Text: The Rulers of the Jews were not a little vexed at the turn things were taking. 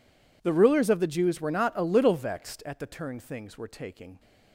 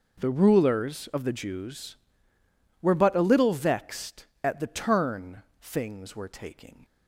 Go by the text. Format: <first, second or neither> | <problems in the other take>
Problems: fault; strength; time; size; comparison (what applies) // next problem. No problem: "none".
first | says "but" for "not"; at 2.9 s // pauses between "turn" and "things"; slight; at 5.4 s; 0.18 s long